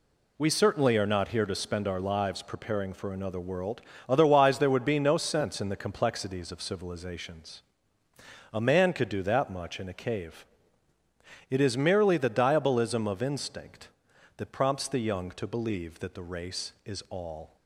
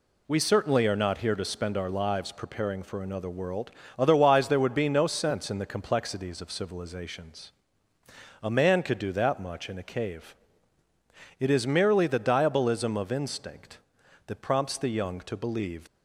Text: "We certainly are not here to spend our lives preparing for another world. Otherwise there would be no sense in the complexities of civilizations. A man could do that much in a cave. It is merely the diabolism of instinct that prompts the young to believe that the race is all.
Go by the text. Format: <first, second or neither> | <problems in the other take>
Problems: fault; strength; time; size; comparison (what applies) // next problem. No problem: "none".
first | stops before "that the race is all"; at 15.8 s